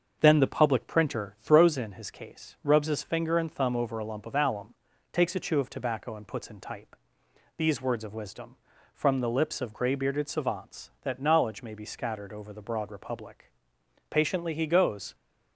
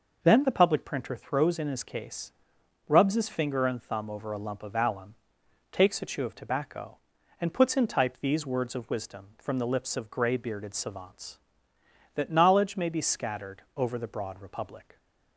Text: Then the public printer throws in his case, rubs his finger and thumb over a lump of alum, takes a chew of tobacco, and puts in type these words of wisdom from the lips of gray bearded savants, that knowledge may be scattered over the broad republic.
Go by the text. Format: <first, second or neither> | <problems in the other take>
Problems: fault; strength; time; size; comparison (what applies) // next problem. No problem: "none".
second | starts louder than the rest; until 1.2 s; 6.5 dB // pauses between "type" and "these"; noticeable; at 6.9 s; 0.62 s long // goes on to say "Patiently he goes"; noticeable; from 14.1 s on; 1.0 s long